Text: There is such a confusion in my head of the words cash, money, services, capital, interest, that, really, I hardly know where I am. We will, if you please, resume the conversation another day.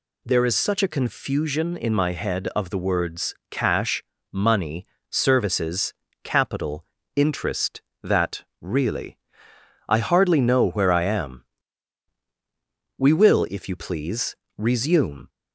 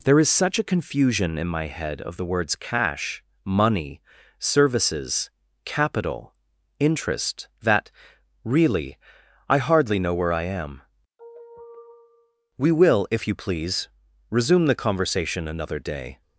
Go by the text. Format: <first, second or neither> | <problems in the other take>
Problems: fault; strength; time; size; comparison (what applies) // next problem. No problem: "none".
second | pauses between "words" and "cash"; slight; at 3.3 s; 0.16 s long // stops before "the conversation another day"; at 15.2 s